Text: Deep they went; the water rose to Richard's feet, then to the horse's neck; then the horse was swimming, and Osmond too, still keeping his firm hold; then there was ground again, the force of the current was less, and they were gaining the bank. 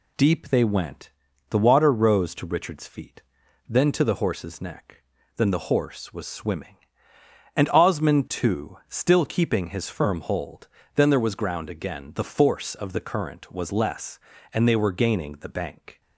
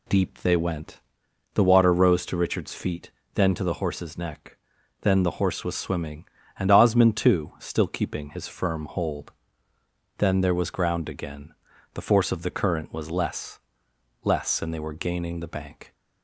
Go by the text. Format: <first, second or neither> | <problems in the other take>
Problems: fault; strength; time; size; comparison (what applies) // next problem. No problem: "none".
first | says "less" twice; at 14.2 s